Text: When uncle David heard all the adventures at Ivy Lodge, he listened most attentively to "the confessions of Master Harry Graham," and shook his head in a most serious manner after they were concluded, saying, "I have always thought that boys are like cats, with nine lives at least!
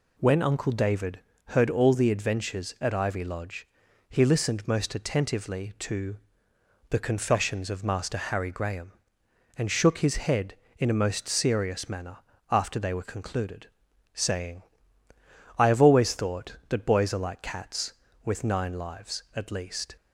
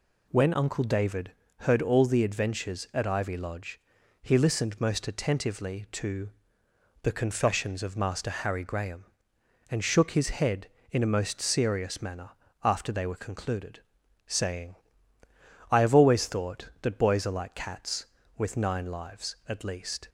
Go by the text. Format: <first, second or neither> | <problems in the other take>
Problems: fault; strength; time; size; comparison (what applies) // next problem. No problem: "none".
neither | pauses between "David" and "heard"; slight; the same in both // pauses between "to" and "the"; noticeable; the same in both // pauses between "manner" and "after"; slight; the same in both